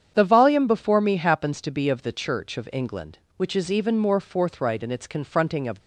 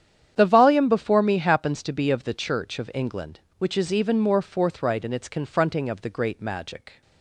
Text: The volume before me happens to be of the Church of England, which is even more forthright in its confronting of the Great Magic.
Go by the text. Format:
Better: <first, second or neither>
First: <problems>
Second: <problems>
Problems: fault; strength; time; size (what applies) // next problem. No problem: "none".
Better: second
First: starts louder than the rest; strong; until 1.1 s; 8 dB // stops before "the Great Magic"; at 5.8 s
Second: starts louder than the rest; strong; until 1.3 s; 9 dB